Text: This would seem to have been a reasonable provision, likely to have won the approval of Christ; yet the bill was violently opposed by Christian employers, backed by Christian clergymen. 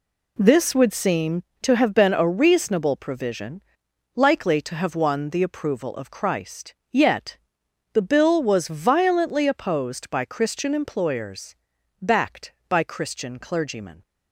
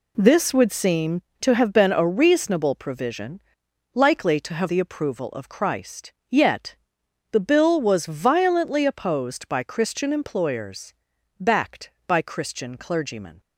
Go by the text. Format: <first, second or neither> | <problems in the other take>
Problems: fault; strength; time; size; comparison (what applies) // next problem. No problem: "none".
first | skips "won"; at 4.6 s // pauses between "yet" and "the"; noticeable; at 6.7 s; 0.56 s long; noticeable in the first